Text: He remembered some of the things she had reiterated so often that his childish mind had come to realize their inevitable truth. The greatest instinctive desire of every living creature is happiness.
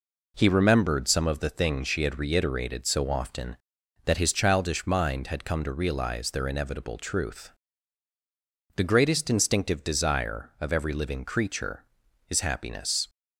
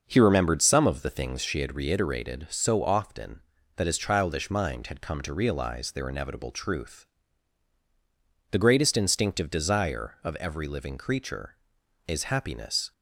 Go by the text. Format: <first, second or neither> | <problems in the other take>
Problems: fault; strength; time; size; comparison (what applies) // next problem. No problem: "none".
first | starts louder than the rest; noticeable; until 1.6 s; 6 dB